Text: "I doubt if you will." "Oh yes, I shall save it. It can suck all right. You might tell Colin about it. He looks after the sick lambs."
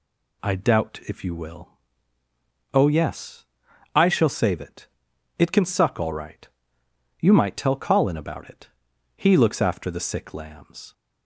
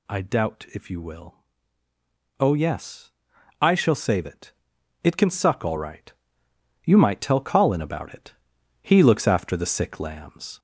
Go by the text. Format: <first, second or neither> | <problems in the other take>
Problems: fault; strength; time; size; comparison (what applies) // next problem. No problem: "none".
first | gets louder; slight; throughout; 3.5 dB